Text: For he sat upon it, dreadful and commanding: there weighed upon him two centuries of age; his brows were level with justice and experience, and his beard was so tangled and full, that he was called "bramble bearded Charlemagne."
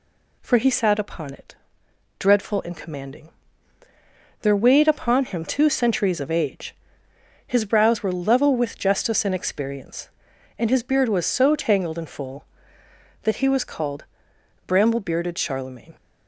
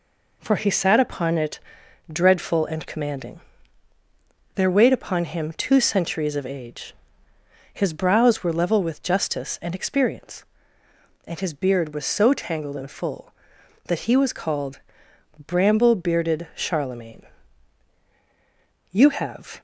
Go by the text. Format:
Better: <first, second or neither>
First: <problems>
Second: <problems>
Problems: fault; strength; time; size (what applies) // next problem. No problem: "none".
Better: first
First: pauses between "called" and "bramble"; noticeable; at 14.0 s; 0.62 s long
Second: pauses between "called" and "bramble"; noticeable; at 14.7 s; 0.66 s long // goes on to say "You have"; noticeable; from 18.9 s on; 0.68 s long